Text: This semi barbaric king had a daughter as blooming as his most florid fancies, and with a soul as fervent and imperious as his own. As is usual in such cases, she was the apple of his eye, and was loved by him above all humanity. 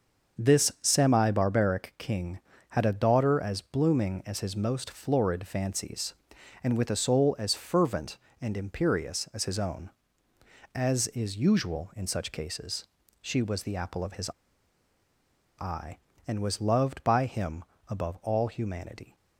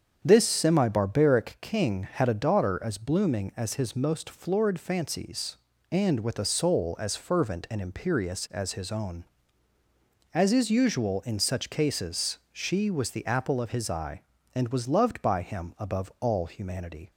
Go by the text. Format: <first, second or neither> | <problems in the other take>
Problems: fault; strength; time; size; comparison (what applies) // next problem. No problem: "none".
second | starts louder than the rest; until 1.4 s; 6.5 dB; strong in the second // pauses between "his" and "eye"; strong; at 14.3 s; 1.2 s long // pauses between "him" and "above"; slight; at 17.6 s; 0.26 s long